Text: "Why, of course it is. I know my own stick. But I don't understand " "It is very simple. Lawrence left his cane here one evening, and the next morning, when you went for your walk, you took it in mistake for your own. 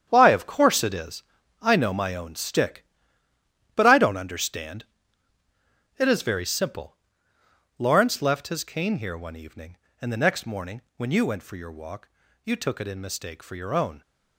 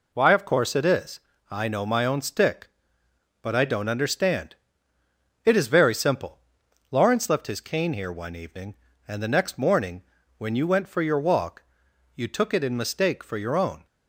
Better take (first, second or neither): second